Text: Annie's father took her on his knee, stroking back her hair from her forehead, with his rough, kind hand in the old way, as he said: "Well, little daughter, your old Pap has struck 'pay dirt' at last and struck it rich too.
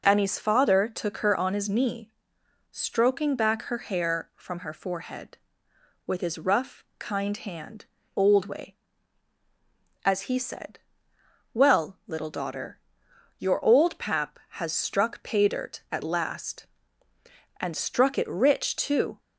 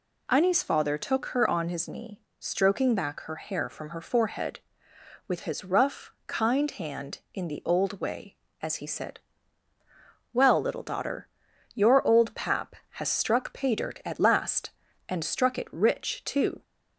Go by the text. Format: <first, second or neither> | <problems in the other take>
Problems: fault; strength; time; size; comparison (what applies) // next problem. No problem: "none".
second | skips "in the"; at 8.0 s